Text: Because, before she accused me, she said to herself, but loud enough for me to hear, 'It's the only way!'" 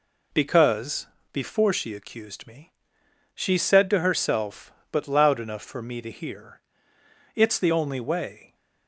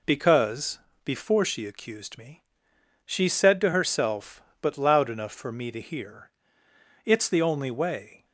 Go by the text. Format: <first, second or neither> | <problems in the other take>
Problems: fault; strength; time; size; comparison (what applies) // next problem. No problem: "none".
neither | none